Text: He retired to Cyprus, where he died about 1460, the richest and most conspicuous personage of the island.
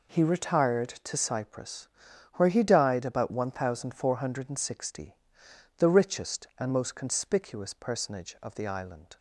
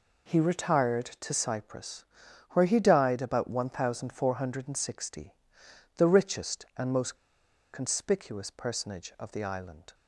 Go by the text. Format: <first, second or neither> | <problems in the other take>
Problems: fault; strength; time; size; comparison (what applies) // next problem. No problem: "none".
first | pauses between "most" and "conspicuous"; noticeable; at 7.1 s; 0.58 s long